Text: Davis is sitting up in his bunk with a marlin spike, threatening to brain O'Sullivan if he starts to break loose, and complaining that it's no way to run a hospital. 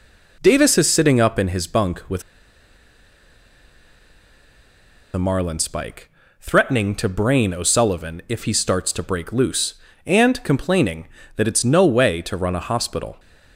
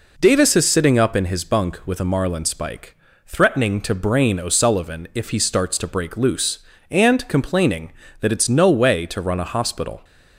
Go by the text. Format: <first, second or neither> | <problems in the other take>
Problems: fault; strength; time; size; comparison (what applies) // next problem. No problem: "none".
second | pauses between "with" and "a"; strong; at 2.2 s; 2.9 s long